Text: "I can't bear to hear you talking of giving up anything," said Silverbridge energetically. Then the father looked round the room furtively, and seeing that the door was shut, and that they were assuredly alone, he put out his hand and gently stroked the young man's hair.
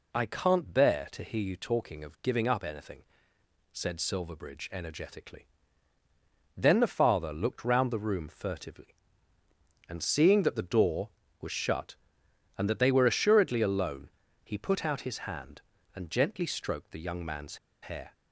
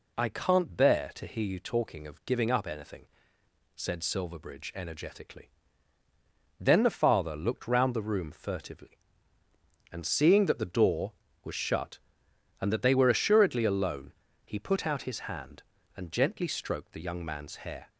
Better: second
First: pauses between "man's" and "hair"; slight; at 17.5 s; 0.25 s long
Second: none

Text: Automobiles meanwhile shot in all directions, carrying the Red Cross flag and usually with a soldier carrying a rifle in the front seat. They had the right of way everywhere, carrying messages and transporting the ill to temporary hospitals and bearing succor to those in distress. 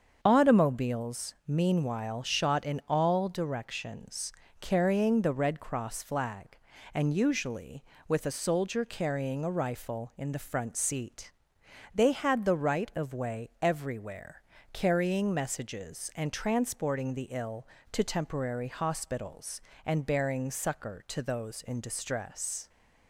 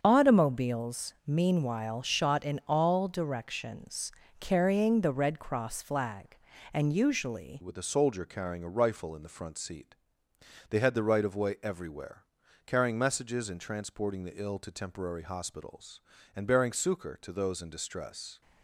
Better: first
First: starts louder than the rest; until 1.2 s; 7 dB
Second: starts louder than the rest; until 1.0 s; 7 dB // changes voice at "with"; from 7.6 s on; 10.8 s long

